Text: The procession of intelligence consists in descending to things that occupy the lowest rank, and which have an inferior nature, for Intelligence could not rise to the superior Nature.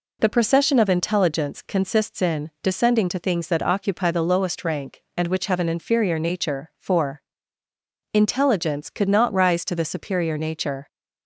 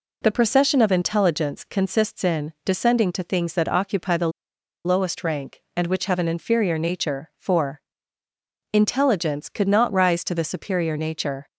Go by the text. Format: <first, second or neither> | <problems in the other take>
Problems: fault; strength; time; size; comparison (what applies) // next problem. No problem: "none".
first | pauses between "the" and "lowest"; noticeable; at 4.2 s; 0.55 s long // pauses between "for" and "Intelligence"; noticeable; at 7.8 s; 0.92 s long; noticeable in the first